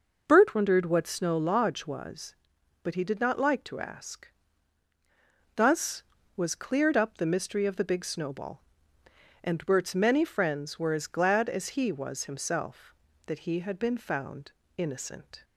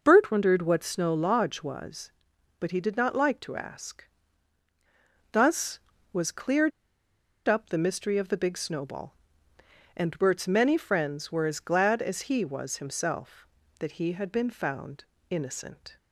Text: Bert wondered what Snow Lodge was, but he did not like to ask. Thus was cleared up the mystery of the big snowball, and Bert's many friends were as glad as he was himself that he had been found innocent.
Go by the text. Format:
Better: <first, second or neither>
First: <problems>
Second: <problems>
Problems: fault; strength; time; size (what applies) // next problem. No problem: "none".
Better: first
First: pauses between "found" and "innocent"; slight; at 14.5 s; 0.26 s long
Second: pauses between "cleared" and "up"; noticeable; at 6.7 s; 0.77 s long // pauses between "found" and "innocent"; slight; at 15.0 s; 0.26 s long